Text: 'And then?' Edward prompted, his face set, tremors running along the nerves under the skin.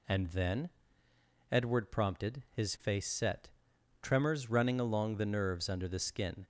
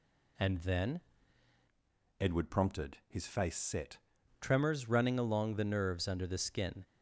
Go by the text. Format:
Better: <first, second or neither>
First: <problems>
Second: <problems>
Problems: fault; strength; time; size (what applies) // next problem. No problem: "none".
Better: first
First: none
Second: changes voice from "Edward" to "set"; from 2.1 to 3.9 s; 1.8 s long